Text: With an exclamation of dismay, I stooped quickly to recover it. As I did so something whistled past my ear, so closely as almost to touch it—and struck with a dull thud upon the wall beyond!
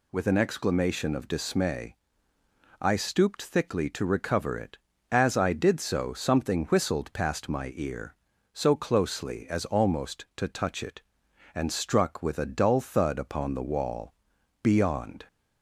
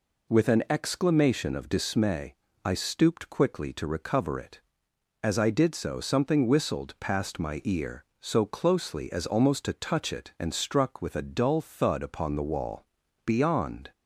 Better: second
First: says "thickly" for "quickly"; at 3.4 s // pauses between "wall" and "beyond"; noticeable; at 14.1 s; 0.50 s long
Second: pauses between "wall" and "beyond"; at 12.8 s; 0.38 s long

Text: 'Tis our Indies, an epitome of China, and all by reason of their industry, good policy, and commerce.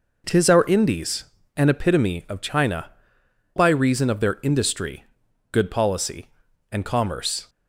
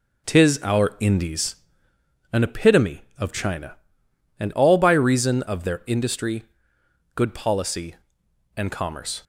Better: second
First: skips "and all"; at 3.2 s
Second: none

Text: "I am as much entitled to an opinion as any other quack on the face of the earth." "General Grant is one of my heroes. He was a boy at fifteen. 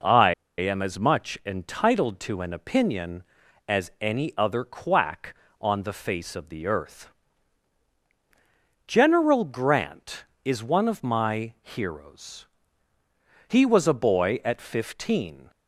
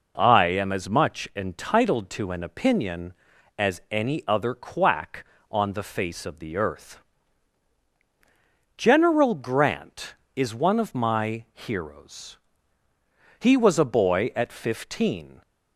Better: second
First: pauses between "I" and "am"; slight; at 0.3 s; 0.26 s long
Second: none

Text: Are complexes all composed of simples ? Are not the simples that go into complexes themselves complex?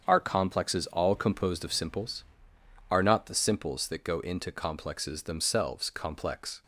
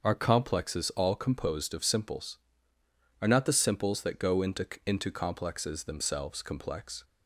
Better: first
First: starts louder than the rest; until 1.0 s; 7 dB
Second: starts louder than the rest; noticeable; until 1.0 s; 6 dB // says "into" twice; at 4.8 s

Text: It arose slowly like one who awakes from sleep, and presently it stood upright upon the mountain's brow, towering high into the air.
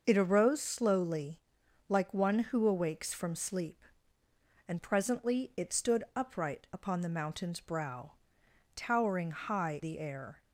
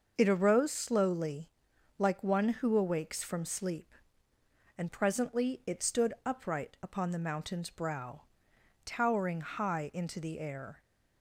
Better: second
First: starts louder than the rest; noticeable; until 1.0 s; 6 dB // pauses between "slowly" and "like"; noticeable; at 1.3 s; 0.50 s long // skips "into"; at 9.8 s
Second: starts louder than the rest; noticeable; until 1.2 s; 6 dB // pauses between "slowly" and "like"; noticeable; at 1.4 s; 0.50 s long

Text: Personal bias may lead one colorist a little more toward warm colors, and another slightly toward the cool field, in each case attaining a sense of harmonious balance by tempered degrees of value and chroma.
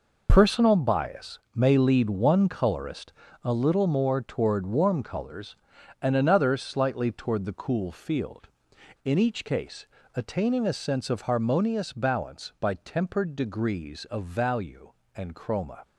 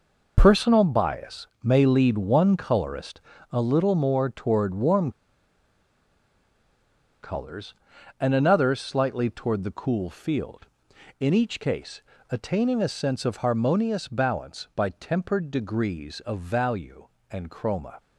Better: first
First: pauses between "colorist" and "a"; slight; at 3.1 s; 0.32 s long // pauses between "case" and "attaining"; slight; at 9.8 s; 0.30 s long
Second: pauses between "colorist" and "a"; slight; at 3.1 s; 0.32 s long // pauses between "warm" and "colors"; strong; at 5.1 s; 2.1 s long // pauses between "case" and "attaining"; slight; at 12.0 s; 0.30 s long

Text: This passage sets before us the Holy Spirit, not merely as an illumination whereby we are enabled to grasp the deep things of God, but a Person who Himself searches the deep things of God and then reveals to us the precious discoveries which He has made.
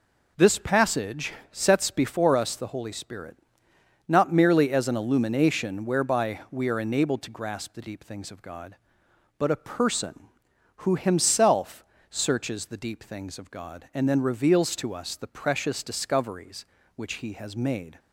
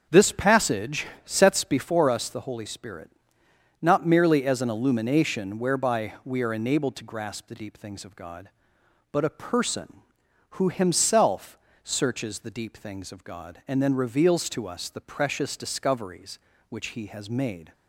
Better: first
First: pauses between "passage" and "sets"; slight; at 1.3 s; 0.20 s long // pauses between "Himself" and "searches"; slight; at 11.8 s; 0.26 s long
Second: starts louder than the rest; strong; until 1.7 s; 7 dB // pauses between "passage" and "sets"; slight; at 1.0 s; 0.20 s long // pauses between "Himself" and "searches"; slight; at 11.5 s; 0.26 s long

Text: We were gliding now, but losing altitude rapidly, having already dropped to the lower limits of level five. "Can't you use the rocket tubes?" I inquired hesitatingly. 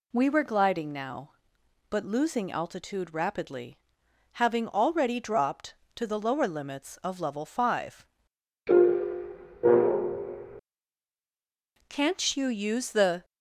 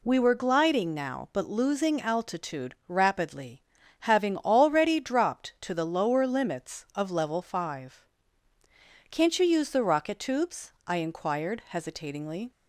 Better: second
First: stops before "rocket tubes I inquired hesitatingly"; at 13.2 s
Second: none

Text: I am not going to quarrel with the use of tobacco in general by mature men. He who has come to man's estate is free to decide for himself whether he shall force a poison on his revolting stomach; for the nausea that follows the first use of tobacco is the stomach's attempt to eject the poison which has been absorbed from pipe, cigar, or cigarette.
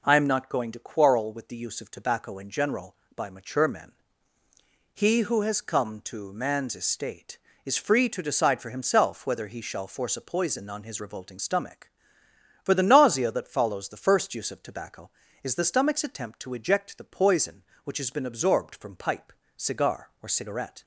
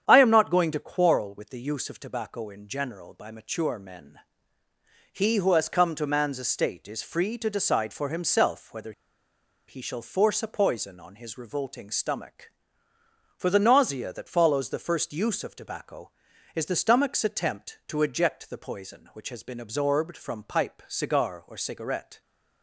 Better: first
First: none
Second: starts louder than the rest; strong; until 1.0 s; 8.5 dB // pauses between "whether" and "he"; noticeable; at 8.9 s; 0.76 s long

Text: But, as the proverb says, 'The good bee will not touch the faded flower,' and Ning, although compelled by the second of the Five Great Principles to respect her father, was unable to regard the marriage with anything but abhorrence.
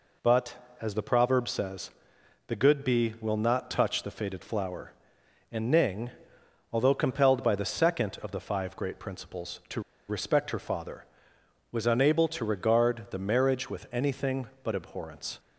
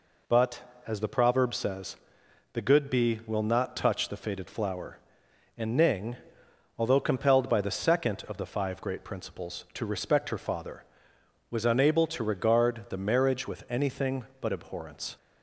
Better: second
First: pauses between "to" and "respect"; slight; at 9.8 s; 0.27 s long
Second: none

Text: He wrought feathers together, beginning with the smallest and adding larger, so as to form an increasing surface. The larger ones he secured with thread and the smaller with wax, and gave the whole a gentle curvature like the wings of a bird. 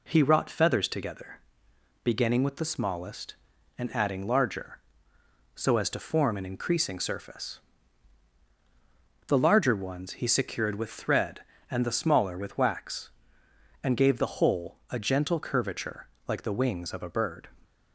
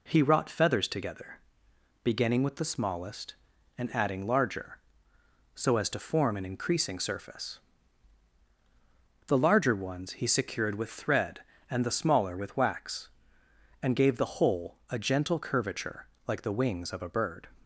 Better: neither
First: pauses between "curvature" and "like"; slight; at 16.0 s; 0.22 s long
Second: pauses between "curvature" and "like"; slight; at 16.0 s; 0.22 s long

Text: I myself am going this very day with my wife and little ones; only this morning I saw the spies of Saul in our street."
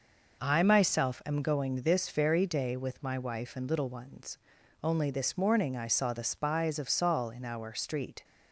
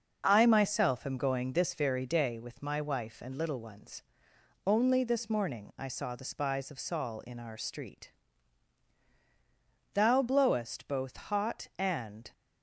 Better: first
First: none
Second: goes on to say "Thou blowest both hot and"; strong; from 9.9 s on; 2.3 s long

